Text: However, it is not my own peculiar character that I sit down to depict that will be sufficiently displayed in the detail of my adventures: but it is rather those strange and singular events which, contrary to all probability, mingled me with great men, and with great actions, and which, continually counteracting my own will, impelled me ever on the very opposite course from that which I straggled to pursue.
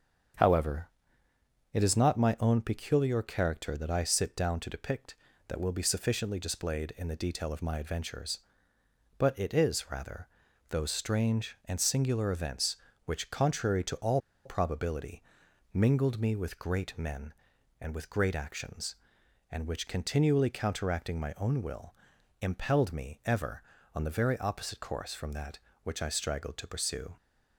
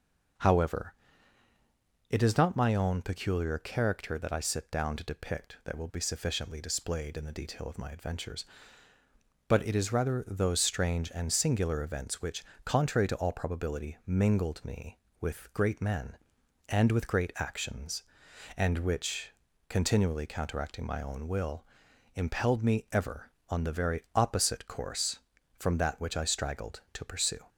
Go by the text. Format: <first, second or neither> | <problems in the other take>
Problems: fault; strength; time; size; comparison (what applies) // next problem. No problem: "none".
second | starts louder than the rest; strong; until 2.2 s; 7.5 dB // pauses between "rather" and "those"; at 10.2 s; 0.40 s long // pauses between "all" and "probability"; slight; at 14.1 s; 0.26 s long